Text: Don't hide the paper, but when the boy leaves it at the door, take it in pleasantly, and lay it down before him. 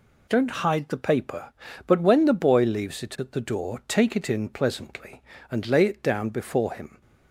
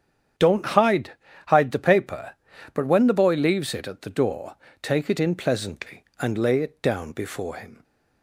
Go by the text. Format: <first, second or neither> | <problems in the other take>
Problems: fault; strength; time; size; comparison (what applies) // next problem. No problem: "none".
first | starts louder than the rest; strong; until 1.7 s; 8.5 dB // says "hide" twice; at 1.4 s